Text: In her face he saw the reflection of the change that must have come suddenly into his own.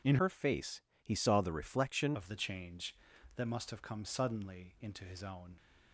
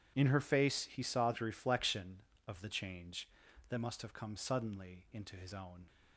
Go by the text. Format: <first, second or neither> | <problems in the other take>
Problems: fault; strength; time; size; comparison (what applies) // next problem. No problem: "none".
second | changes voice from "her" to "reflection"; from 0.2 to 2.1 s; 1.9 s long // pauses between "face" and "he"; slight; at 0.8 s; 0.20 s long